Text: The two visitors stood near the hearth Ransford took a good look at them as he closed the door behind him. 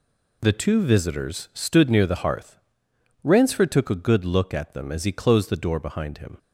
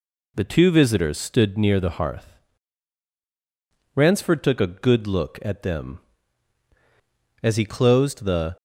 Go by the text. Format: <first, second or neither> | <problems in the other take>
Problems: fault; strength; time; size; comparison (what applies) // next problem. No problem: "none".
first | pauses between "hearth" and "Ransford"; strong; at 2.3 s; 1.5 s long; noticeable in the first // stops before "door behind him"; at 8.5 s